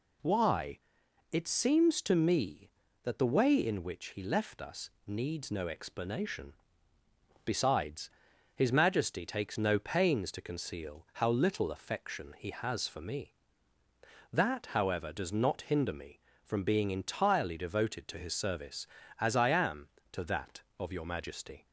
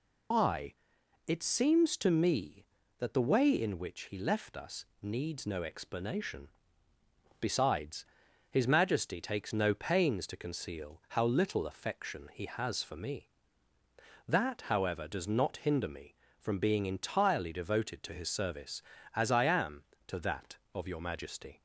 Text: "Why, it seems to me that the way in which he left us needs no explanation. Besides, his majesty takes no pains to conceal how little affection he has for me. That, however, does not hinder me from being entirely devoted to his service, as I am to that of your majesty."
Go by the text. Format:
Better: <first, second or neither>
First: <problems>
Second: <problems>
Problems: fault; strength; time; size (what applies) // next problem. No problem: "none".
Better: first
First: pauses between "us" and "needs"; slight; at 4.8 s; 0.16 s long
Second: loses the start of "Why"; at 0.3 s; 135 ms // pauses between "us" and "needs"; slight; at 4.8 s; 0.16 s long